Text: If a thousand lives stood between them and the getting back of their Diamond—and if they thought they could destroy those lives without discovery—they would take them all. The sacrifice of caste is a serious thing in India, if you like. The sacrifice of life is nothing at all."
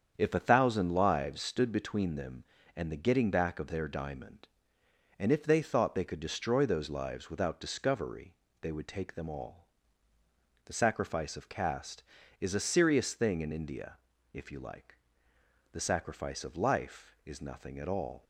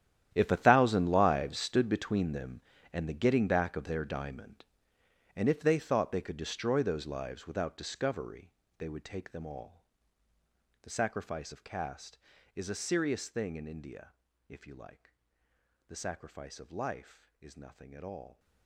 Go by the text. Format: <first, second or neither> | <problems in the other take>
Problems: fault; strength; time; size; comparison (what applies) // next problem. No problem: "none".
first | gets quieter; strong; throughout; 17 dB // starts louder than the rest; strong; until 1.3 s; 11 dB; strong in the first